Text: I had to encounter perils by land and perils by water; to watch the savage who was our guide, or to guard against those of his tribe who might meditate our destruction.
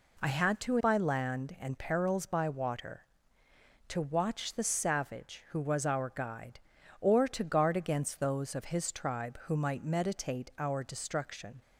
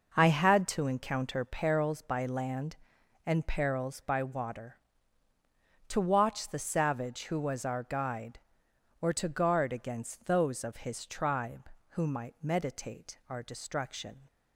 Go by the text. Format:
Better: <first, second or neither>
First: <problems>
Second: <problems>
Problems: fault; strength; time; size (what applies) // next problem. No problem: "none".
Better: second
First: skips "encounter perils"; at 0.7 s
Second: none